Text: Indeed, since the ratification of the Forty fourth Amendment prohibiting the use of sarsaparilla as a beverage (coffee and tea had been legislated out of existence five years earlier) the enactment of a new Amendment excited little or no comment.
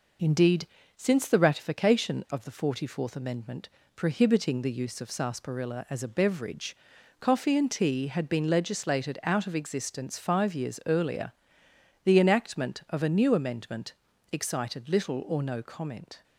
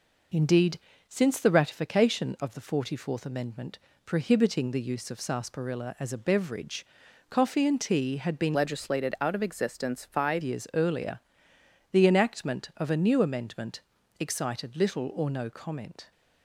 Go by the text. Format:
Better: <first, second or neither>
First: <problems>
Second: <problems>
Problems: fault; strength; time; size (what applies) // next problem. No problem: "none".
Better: first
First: pauses between "Amendment" and "prohibiting"; slight; at 3.6 s; 0.30 s long // pauses between "Amendment" and "excited"; slight; at 13.9 s; 0.36 s long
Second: pauses between "Amendment" and "prohibiting"; slight; at 3.7 s; 0.30 s long // changes voice from "legislated" to "five"; from 8.5 to 10.4 s; 1.9 s long // pauses between "Amendment" and "excited"; slight; at 13.8 s; 0.36 s long